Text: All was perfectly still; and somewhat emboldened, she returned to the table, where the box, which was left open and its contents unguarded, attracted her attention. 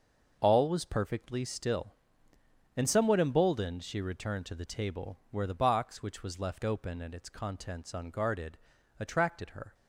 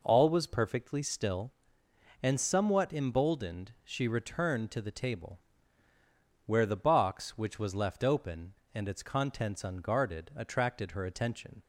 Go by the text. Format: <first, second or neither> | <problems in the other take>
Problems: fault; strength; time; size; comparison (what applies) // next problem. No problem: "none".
second | stops before "attention"; at 9.7 s